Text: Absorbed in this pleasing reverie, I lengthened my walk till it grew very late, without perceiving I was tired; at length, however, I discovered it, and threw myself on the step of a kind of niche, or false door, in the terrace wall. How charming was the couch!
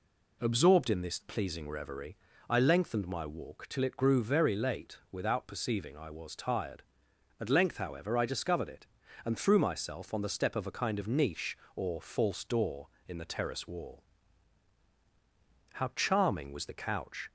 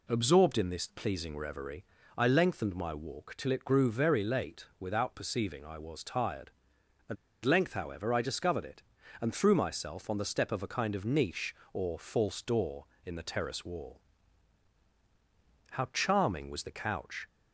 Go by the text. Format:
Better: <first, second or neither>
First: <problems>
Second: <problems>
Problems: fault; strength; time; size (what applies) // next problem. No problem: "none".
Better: first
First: none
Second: pauses between "at" and "length"; slight; at 7.1 s; 0.29 s long